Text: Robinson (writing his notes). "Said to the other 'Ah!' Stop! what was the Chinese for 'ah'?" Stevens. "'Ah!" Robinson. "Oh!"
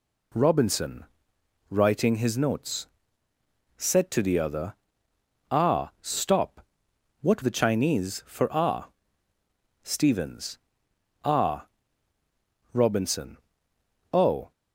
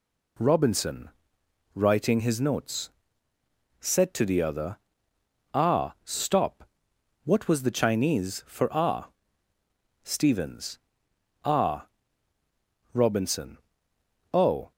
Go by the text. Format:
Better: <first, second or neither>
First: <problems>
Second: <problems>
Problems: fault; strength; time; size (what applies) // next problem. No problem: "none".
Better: second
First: pauses between "other" and "Ah"; noticeable; at 4.7 s; 0.78 s long // skips "was"; at 7.4 s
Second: pauses between "other" and "Ah"; noticeable; at 4.7 s; 0.78 s long